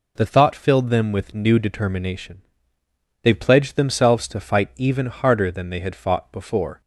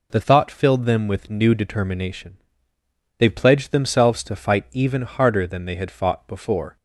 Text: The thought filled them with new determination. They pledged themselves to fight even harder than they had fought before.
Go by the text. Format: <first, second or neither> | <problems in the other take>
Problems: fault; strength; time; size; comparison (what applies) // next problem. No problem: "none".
neither | none